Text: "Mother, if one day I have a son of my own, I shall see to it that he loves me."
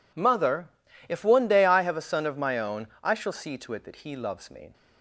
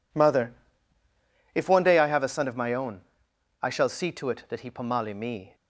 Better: first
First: none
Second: says "pomali" for "loves"; at 4.7 s

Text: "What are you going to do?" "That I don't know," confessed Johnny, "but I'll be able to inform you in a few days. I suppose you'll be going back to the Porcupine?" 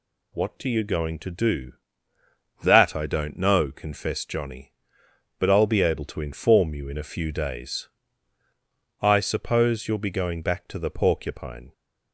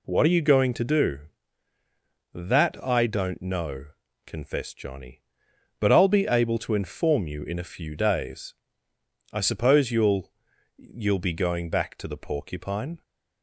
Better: first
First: none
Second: says "you'll" twice; at 10.7 s

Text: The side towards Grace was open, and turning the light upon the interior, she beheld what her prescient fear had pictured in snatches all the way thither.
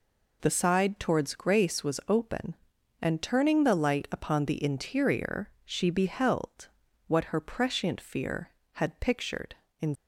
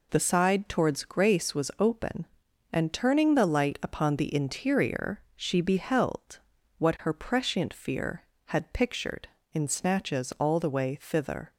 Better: second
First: pauses between "beheld" and "what"; at 6.6 s; 0.40 s long // stops before "snatches all the way thither"; at 9.9 s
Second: pauses between "beheld" and "what"; at 6.3 s; 0.40 s long

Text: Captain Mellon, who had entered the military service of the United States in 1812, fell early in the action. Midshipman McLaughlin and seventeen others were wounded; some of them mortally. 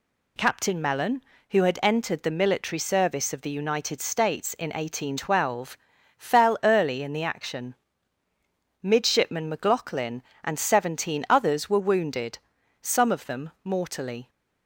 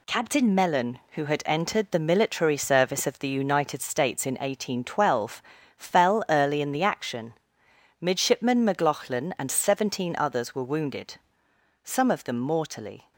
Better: first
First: none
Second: gets quieter; noticeable; throughout; 6 dB

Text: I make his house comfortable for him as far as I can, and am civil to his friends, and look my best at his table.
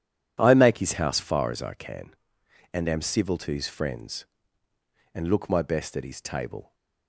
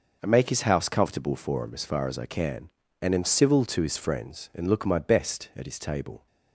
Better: second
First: skips "comfortable for him as"; at 1.1 s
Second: none

